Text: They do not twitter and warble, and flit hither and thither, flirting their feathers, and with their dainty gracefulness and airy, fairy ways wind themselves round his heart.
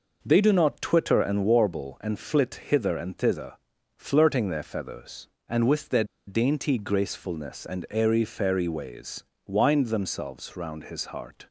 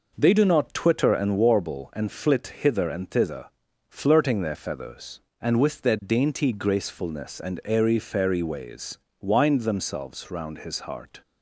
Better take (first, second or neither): second